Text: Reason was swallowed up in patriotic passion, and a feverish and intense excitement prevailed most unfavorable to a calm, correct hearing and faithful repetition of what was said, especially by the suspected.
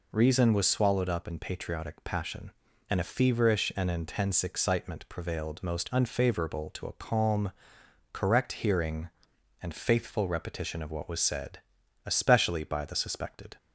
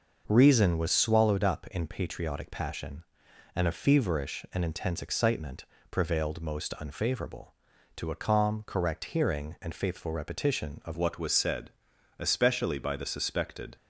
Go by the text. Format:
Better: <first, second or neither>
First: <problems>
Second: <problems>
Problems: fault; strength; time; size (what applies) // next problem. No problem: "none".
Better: first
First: none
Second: pauses between "excitement" and "prevailed"; slight; at 5.6 s; 0.28 s long // changes voice at "what"; from 10.9 s on; 2.8 s long